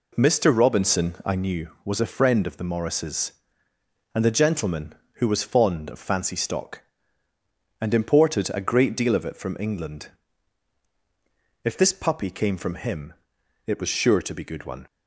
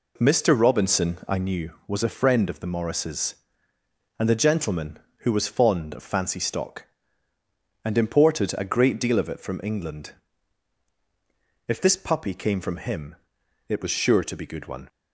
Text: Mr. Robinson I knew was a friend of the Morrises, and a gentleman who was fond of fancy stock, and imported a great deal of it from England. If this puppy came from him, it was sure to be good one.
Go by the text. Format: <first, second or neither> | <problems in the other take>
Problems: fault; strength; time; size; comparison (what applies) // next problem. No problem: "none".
neither | none